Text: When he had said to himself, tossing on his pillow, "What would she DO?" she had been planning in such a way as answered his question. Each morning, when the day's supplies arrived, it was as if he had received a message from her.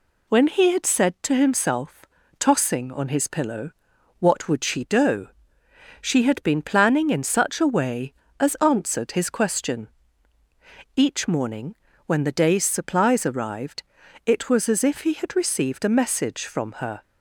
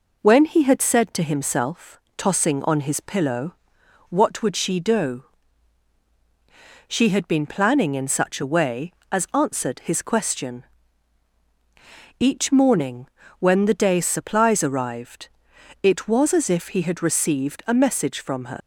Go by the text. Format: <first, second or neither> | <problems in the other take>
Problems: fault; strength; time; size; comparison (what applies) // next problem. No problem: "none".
first | leaves "her" unfinished; at 18.6 s; 105 ms